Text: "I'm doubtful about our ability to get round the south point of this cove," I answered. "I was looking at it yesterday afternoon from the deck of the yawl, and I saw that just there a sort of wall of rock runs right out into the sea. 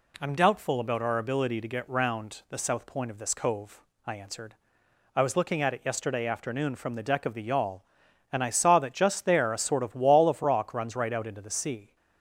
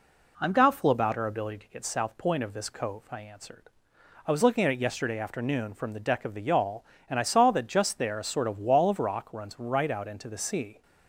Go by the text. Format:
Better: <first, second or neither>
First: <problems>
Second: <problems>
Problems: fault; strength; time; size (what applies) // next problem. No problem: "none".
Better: first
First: none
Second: skips "round the"; at 1.8 s